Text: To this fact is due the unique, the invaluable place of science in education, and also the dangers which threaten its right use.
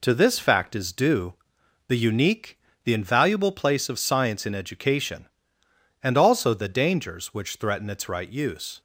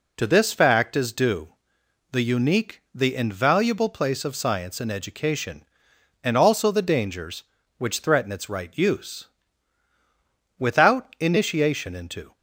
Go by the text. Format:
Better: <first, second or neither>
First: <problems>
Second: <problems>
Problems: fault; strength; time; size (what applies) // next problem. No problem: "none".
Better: first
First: pauses between "due" and "the"; noticeable; at 1.3 s; 0.54 s long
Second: pauses between "due" and "the"; noticeable; at 1.4 s; 0.62 s long // goes on to say "Without initiation into"; strong; from 10.5 s on; 1.7 s long